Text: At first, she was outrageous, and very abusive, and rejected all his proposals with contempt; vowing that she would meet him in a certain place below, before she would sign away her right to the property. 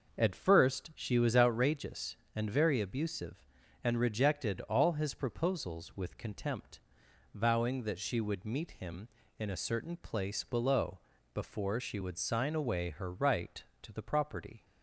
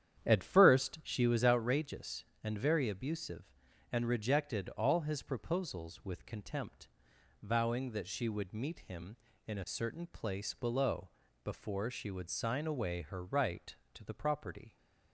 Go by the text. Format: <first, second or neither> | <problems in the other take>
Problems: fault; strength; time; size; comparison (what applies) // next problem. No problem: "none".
first | starts louder than the rest; strong; until 1.3 s; 9.5 dB